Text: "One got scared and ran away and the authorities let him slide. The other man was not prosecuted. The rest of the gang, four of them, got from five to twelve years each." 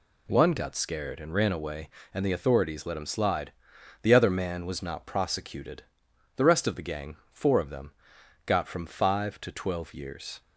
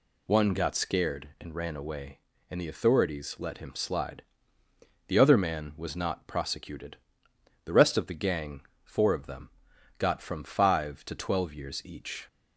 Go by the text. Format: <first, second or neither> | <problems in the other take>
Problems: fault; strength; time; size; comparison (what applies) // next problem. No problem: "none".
second | stops before "each"; at 10.4 s